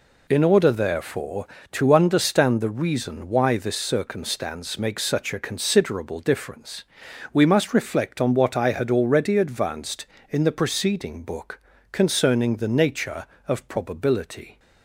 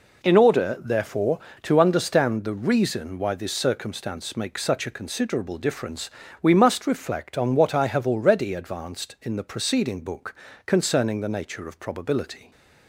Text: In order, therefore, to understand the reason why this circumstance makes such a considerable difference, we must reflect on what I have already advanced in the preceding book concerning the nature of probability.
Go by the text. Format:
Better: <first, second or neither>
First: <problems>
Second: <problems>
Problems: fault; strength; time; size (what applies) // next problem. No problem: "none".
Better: second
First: says "had" for "have"; at 8.7 s // pauses between "book" and "concerning"; slight; at 11.6 s; 0.32 s long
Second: pauses between "book" and "concerning"; slight; at 10.3 s; 0.32 s long